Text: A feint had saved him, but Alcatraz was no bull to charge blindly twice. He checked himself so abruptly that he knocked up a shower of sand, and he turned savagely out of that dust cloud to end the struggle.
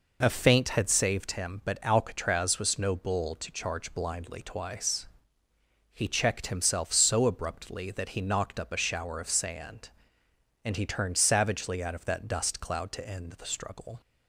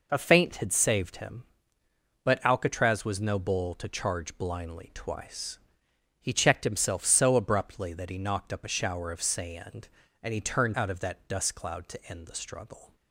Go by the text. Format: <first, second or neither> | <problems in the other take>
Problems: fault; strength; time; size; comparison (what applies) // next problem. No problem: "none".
first | skips "savagely"; at 10.7 s